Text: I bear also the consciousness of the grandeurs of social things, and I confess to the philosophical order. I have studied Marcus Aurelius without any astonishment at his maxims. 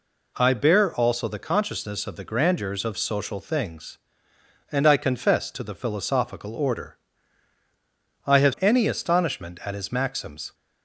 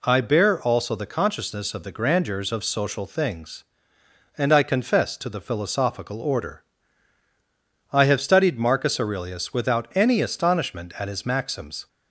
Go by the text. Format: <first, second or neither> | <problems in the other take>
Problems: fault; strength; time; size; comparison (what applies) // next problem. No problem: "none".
second | skips "studied Marcus Aurelius without"; at 8.5 s